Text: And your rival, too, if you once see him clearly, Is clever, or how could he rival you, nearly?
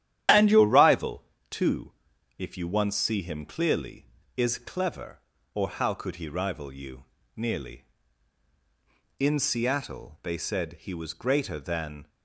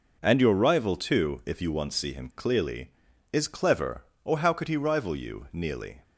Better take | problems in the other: second | starts louder than the rest; strong; until 1.5 s; 10.5 dB // goes on to say "In Seattle they said he was greater than"; strong; from 9.1 s on; 2.9 s long

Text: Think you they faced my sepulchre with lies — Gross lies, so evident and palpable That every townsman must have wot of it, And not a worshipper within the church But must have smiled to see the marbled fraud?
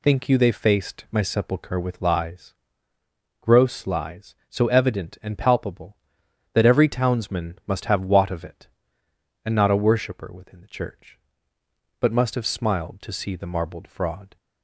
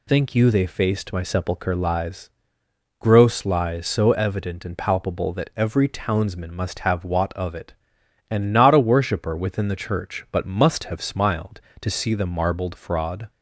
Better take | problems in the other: first | skips "with"; at 1.7 s

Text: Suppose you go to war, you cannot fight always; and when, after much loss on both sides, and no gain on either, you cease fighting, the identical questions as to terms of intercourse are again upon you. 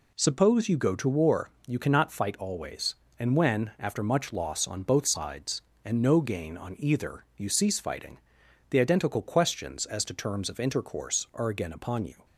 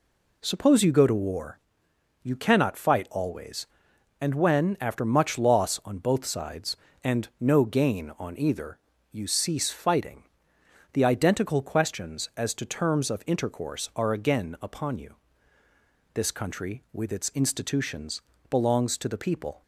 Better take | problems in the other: first | goes on to say "This country with its institutions belongs to the people"; strong; from 16.1 s on; 3.4 s long

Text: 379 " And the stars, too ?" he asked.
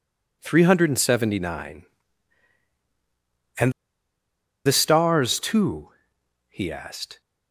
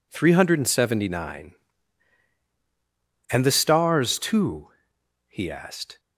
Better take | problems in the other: second | pauses between "And" and "the"; noticeable; at 3.7 s; 0.94 s long

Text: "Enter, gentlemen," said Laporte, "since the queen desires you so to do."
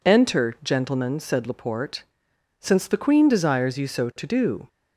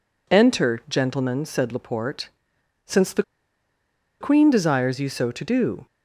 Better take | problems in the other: first | pauses between "the" and "queen"; noticeable; at 3.2 s; 0.97 s long

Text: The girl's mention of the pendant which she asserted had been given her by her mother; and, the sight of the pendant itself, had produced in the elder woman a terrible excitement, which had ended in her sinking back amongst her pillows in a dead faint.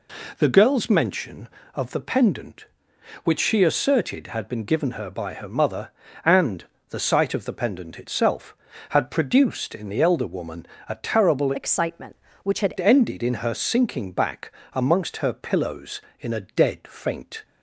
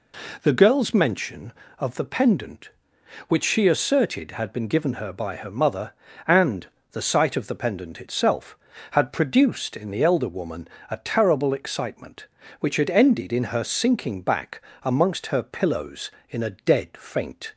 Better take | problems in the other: second | pauses between "woman" and "a"; slight; at 10.6 s; 0.22 s long; slight in the second // changes voice from "excitement" to "had"; from 11.5 to 12.7 s; 1.2 s long // pauses between "back" and "amongst"; slight; at 14.5 s; 0.22 s long; slight in the second

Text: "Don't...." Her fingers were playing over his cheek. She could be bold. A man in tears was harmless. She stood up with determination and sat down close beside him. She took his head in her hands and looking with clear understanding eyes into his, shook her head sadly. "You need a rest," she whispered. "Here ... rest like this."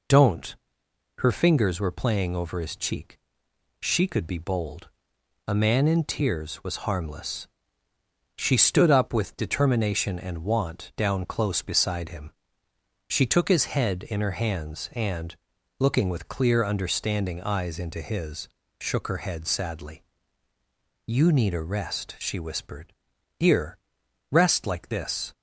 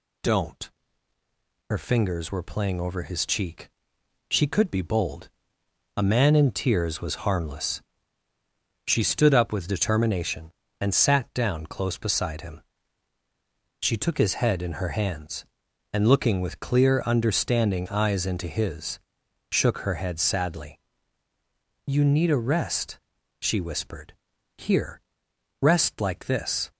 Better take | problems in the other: second | says "want" for "sat"; at 10.4 s // pauses between "and" and "looking"; at 15.3 s; 0.42 s long

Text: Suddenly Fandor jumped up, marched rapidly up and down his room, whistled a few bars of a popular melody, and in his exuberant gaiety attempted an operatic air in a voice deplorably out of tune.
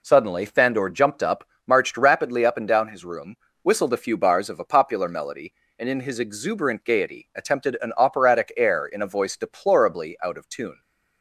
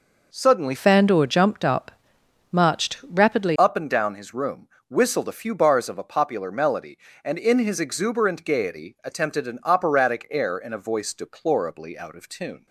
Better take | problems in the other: first | changes voice from "Fandor" to "rapidly"; from 0.7 to 3.5 s; 2.8 s long

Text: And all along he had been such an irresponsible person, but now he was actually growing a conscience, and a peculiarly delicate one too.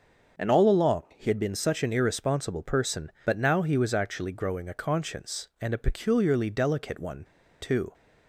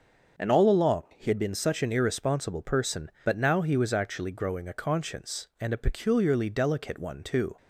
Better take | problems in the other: second | starts louder than the rest; until 1.5 s; 6.5 dB; also in the second // pauses between "one" and "too"; at 7.2 s; 0.37 s long

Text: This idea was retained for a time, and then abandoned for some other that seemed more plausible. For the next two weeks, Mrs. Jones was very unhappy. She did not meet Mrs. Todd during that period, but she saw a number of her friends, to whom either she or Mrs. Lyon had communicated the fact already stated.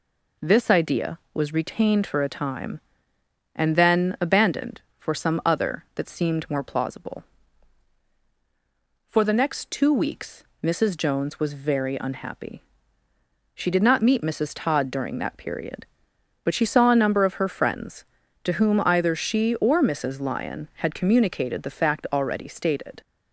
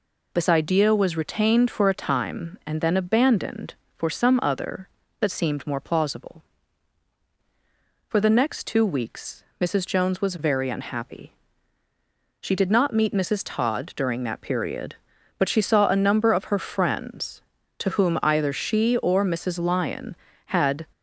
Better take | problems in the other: first | stops before "communicated the fact already stated"; at 20.9 s

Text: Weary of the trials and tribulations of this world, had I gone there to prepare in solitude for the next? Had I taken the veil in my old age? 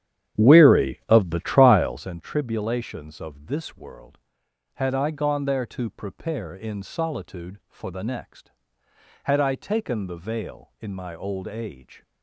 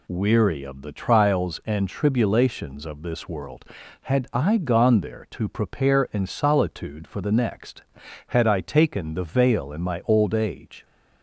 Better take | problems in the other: second | starts louder than the rest; strong; until 2.2 s; 10 dB

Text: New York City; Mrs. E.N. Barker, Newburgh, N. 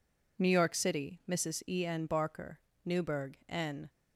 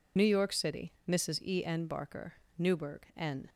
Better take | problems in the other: first | loses the start of "New"; at 0.1 s; 50 ms

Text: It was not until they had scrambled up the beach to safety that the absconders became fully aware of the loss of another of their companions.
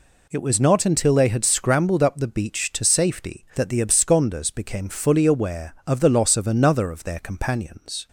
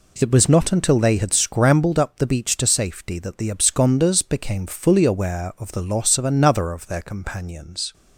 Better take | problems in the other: neither | none

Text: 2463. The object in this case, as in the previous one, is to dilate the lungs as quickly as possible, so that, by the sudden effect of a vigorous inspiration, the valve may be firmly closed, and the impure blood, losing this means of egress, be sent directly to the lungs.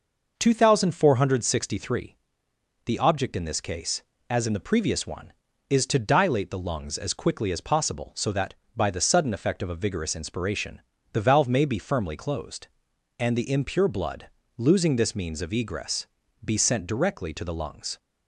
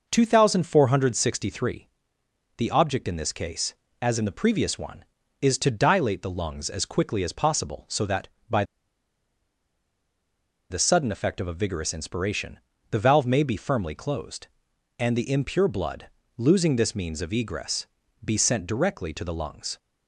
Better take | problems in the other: first | pauses between "by" and "the"; strong; at 8.6 s; 2.0 s long

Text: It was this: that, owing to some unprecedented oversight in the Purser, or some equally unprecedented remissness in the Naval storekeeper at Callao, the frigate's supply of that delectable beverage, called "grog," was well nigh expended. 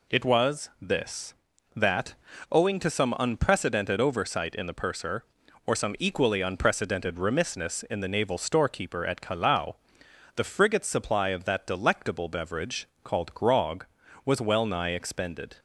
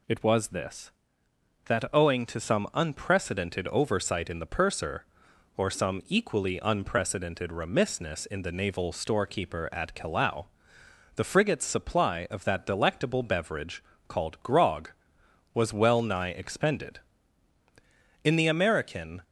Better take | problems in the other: first | goes on to say "In the American"; noticeable; from 18.2 s on; 0.98 s long

